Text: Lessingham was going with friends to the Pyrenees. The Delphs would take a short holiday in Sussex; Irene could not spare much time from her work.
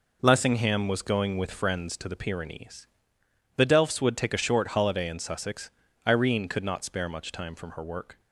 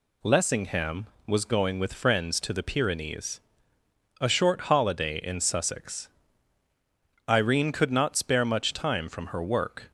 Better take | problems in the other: first | skips "The Delphs would take"; at 3.8 s

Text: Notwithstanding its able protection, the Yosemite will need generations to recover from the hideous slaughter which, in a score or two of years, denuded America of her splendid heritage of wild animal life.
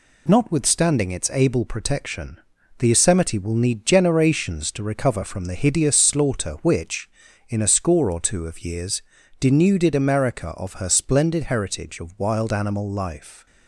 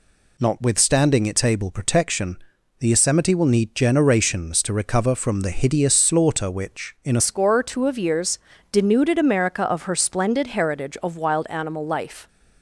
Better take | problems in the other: first | changes voice at "score"; from 7.1 s on; 5.1 s long

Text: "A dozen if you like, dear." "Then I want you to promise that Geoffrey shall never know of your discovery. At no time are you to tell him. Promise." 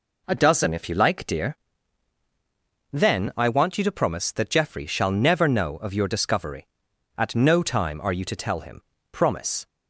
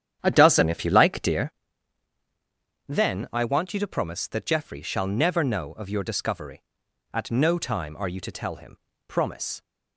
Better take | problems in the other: first | starts louder than the rest; strong; until 1.6 s; 9.5 dB

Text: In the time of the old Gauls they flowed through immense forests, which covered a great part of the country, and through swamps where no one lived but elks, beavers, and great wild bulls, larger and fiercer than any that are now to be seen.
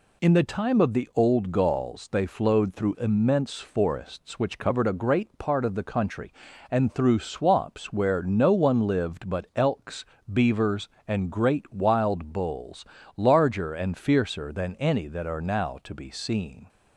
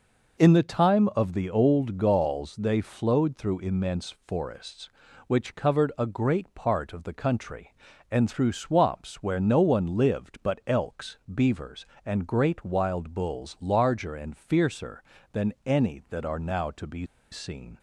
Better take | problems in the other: first | pauses between "be" and "seen"; slight; at 17.0 s; 0.25 s long

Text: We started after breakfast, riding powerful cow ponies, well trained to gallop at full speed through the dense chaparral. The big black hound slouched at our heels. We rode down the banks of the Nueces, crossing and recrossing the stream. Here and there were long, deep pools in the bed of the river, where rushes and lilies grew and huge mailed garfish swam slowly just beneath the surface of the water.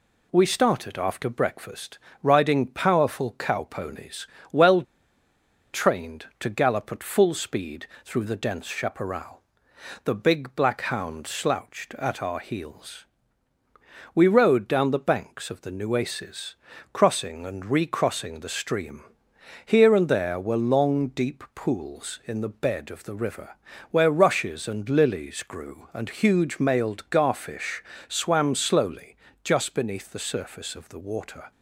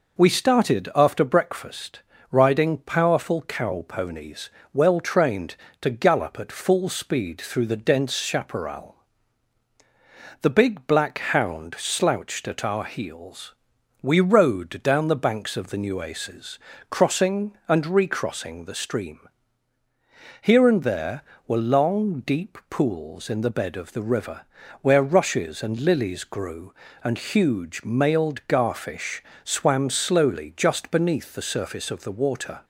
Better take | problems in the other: second | pauses between "well" and "trained"; noticeable; at 4.8 s; 0.90 s long // pauses between "speed" and "through"; slight; at 7.8 s; 0.18 s long // pauses between "garfish" and "swam"; slight; at 27.8 s; 0.24 s long; slight in the second // pauses between "slowly" and "just"; slight; at 29.1 s; 0.28 s long

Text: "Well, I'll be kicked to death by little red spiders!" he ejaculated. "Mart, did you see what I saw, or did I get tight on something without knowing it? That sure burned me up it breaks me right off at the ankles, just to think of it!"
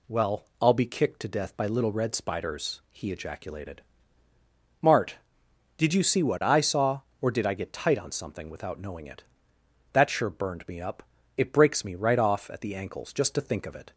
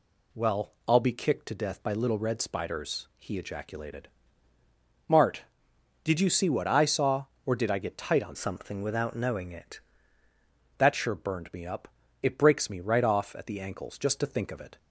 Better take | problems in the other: first | changes voice from "something" to "it"; from 8.3 to 9.7 s; 1.4 s long // pauses between "up" and "it"; slight; at 11.8 s; 0.34 s long; slight in the first

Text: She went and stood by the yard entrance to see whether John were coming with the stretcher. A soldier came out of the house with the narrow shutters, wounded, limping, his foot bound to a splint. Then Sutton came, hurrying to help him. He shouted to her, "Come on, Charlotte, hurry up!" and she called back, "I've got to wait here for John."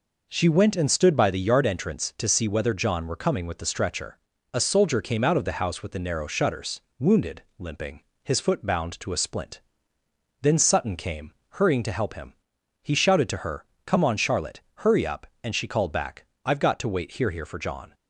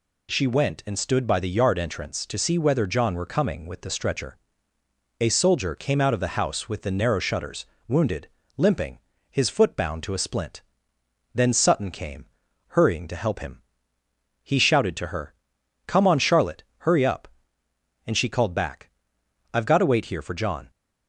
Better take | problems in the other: second | says "here" twice; at 17.2 s

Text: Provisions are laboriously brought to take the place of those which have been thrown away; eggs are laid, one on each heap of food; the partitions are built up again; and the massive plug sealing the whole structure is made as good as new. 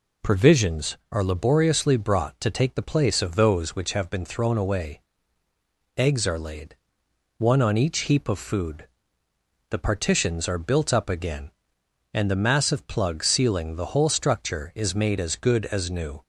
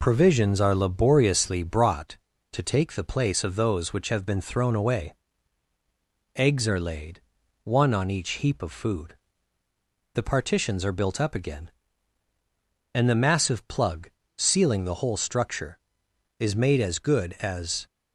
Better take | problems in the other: first | pauses between "plug" and "sealing"; slight; at 14.0 s; 0.28 s long // stops before "new"; at 17.8 s

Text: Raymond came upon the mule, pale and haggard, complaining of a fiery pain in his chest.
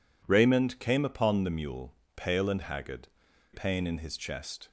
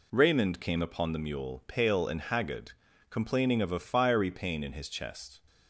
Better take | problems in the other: second | skips "complaining of a fiery"; at 3.3 s

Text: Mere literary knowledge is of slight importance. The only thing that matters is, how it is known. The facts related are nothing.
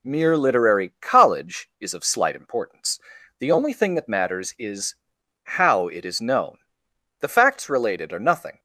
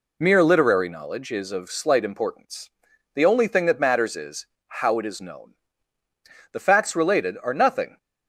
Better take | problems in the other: second | says "college" for "knowledge"; at 1.0 s

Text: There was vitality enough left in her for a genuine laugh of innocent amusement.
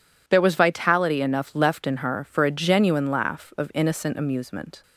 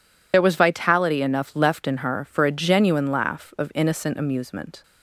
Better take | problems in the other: first | loses the start of "There"; at 0.3 s; 55 ms

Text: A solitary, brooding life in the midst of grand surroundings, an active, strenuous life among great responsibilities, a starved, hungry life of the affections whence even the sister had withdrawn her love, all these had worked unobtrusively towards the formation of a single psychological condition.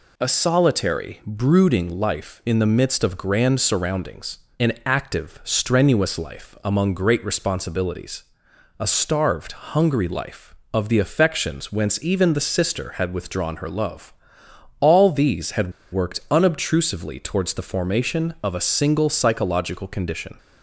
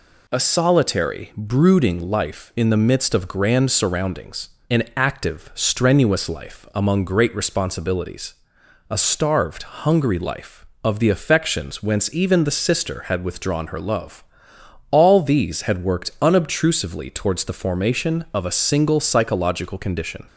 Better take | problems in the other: second | pauses between "had" and "worked"; slight; at 15.7 s; 0.21 s long

